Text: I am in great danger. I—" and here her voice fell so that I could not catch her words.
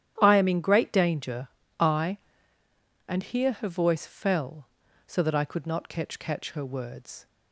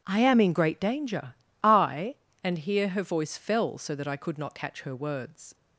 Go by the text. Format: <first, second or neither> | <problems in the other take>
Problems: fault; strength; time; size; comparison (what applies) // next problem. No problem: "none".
second | starts louder than the rest; strong; until 1.2 s; 11 dB // says "catch" twice; at 6.1 s